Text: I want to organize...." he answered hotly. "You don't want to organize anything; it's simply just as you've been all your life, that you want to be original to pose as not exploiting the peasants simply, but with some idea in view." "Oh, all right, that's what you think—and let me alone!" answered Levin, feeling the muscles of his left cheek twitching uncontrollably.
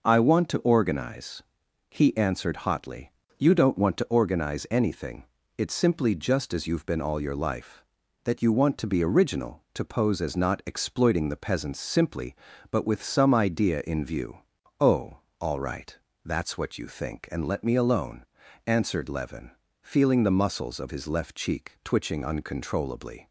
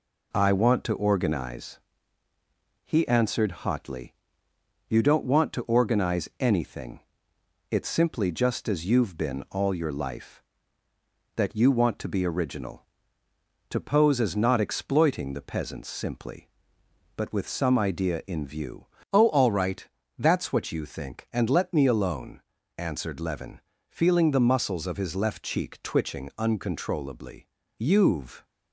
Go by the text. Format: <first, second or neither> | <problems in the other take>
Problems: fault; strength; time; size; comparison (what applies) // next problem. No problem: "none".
first | goes on to say "You've"; noticeable; from 27.7 s on; 0.66 s long